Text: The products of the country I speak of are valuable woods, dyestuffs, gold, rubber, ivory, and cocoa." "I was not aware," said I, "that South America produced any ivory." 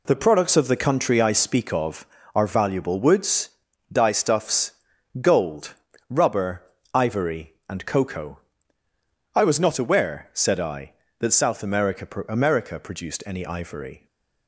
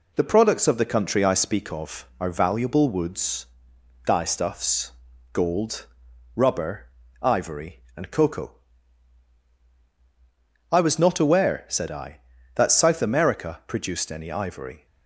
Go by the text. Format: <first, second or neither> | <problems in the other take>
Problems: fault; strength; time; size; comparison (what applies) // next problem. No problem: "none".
second | says "America" twice; at 12.2 s // stays silent after the last word; slight; from 13.9 s on; 0.5 s long